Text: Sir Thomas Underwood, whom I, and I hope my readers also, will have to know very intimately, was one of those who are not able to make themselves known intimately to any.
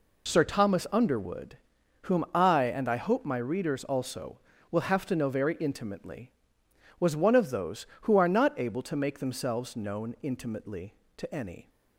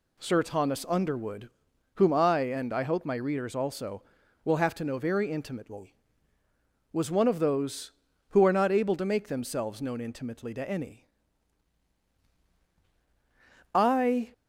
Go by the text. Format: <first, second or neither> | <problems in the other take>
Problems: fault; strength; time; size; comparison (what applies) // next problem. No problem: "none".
first | goes on to say "I"; from 13.7 s on; 0.60 s long